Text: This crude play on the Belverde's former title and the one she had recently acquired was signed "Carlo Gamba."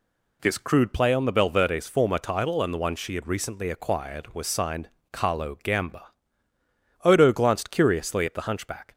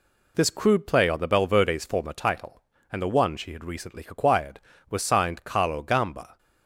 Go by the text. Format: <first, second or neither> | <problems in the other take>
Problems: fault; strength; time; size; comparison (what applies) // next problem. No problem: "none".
second | pauses between "signed" and "Carlo"; slight; at 4.8 s; 0.24 s long // goes on to say "Odo glanced curiously at the hunchback"; strong; from 7.0 s on; 1.9 s long